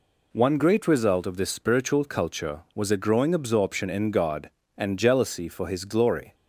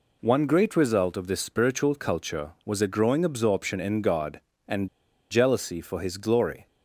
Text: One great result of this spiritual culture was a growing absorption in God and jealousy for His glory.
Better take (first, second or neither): first